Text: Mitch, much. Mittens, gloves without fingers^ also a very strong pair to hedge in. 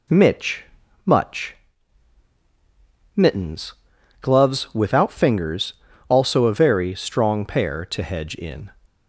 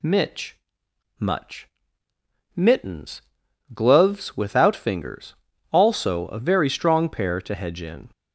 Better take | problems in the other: neither | pauses between "fingers" and "also"; slight; the same in both

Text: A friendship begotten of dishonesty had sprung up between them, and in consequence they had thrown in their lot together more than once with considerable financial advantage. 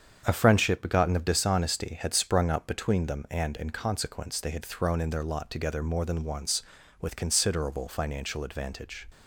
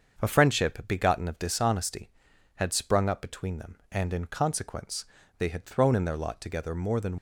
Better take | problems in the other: first | starts louder than the rest; until 1.2 s; 7 dB; strong in the first // pauses between "consequence" and "they"; slight; at 5.0 s; 0.32 s long // stops before "once with considerable financial advantage"; at 7.1 s

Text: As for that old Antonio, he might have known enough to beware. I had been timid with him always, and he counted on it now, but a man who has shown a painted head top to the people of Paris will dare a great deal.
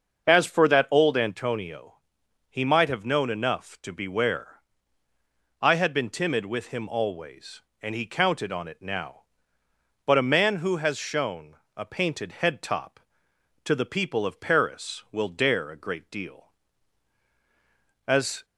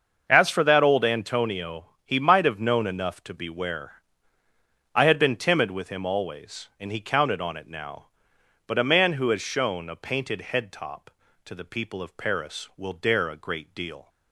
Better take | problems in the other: second | starts louder than the rest; until 1.2 s; 6.5 dB; also in the second // pauses between "shown" and "a"; slight; at 11.5 s; 0.20 s long // goes on to say "As"; slight; from 18.0 s on; 0.38 s long

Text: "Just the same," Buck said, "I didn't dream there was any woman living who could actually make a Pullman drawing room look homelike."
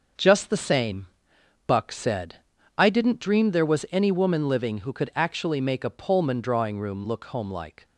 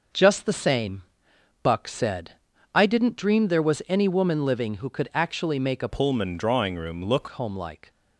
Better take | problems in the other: first | starts louder than the rest; noticeable; until 1.7 s; 6 dB; also in the first // changes voice from "Pullman" to "look"; from 5.8 to 7.2 s; 1.4 s long

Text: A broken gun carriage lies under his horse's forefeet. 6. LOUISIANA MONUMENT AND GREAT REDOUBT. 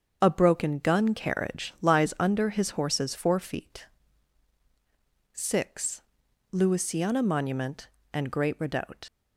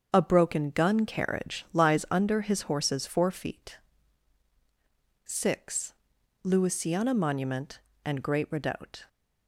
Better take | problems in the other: second | starts louder than the rest; until 1.2 s; 6.5 dB; also in the second // leaves "REDOUBT" unfinished; at 9.0 s; 80 ms

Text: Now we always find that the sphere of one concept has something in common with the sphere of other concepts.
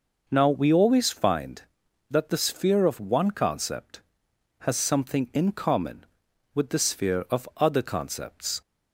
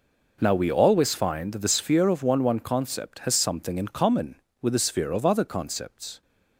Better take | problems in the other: first | says "one" twice; at 2.4 s

